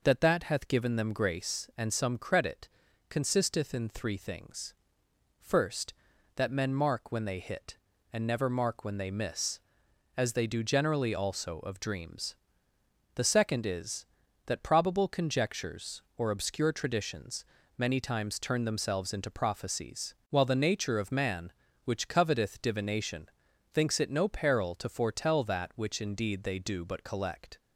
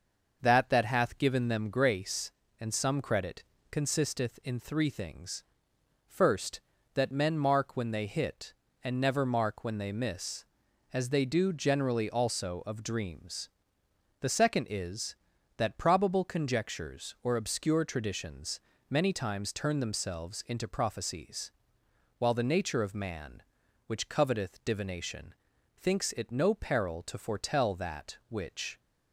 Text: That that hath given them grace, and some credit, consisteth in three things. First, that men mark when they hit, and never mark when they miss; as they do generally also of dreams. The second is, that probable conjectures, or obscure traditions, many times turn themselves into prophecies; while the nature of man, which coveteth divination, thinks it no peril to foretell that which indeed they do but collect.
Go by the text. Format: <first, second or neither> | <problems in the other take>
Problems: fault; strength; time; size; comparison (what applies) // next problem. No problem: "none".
first | starts louder than the rest; noticeable; until 1.4 s; 6 dB // stops before "indeed they do but collect"; at 28.7 s